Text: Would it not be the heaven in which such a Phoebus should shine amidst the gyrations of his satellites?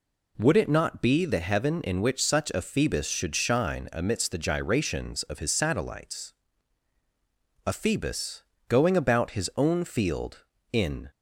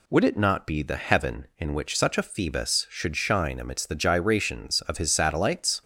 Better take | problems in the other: second | goes on to say "A Phoebus going about his own field in"; strong; from 7.6 s on; 3.4 s long

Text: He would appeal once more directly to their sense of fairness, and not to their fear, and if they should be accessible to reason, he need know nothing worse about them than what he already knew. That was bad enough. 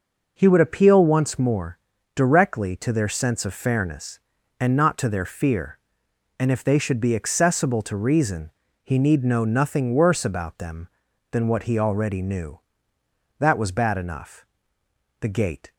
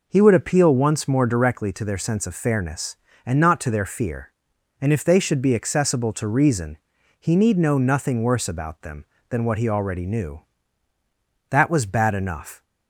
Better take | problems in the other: second | pauses between "more" and "directly"; slight; at 1.7 s; 0.36 s long // goes on to say "The gate"; from 15.1 s on; 0.54 s long

